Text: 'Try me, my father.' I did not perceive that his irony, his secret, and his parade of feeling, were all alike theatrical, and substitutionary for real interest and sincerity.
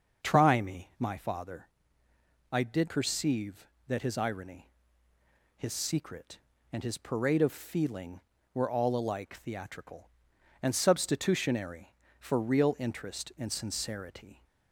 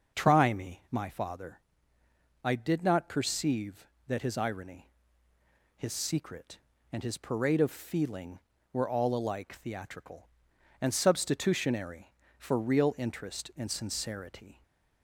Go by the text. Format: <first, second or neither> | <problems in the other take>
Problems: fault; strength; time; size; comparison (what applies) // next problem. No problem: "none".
second | starts louder than the rest; until 1.3 s; 6.5 dB; also in the second // skips "not"; at 2.8 s